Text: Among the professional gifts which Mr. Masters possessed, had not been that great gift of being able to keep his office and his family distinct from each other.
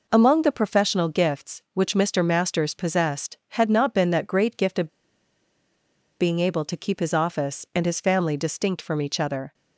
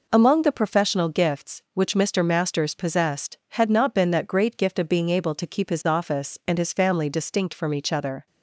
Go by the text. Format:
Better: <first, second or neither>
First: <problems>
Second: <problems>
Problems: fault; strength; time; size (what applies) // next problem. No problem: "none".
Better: second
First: pauses between "of" and "being"; strong; at 4.8 s; 1.3 s long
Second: none